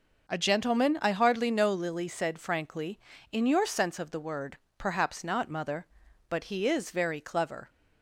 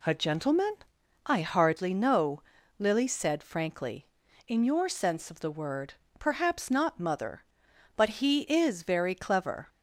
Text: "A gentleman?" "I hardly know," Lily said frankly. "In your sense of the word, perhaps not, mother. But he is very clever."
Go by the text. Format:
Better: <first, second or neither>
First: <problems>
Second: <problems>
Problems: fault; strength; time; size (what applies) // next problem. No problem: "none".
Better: neither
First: none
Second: none